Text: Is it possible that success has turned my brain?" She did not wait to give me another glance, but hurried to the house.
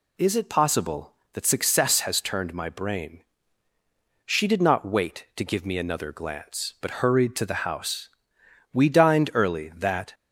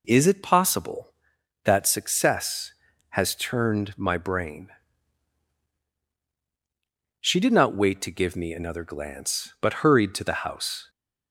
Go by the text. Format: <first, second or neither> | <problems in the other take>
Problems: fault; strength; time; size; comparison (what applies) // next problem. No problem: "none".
second | goes on to say "We dined early that"; from 8.7 s on; 1.4 s long